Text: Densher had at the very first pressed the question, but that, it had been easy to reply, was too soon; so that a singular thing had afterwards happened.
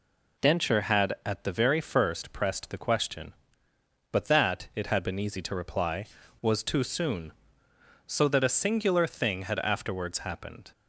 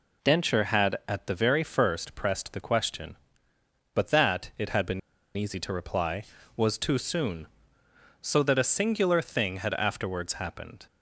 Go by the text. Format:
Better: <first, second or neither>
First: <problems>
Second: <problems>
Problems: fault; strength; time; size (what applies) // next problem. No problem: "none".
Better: first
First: none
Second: pauses between "been" and "easy"; at 4.9 s; 0.37 s long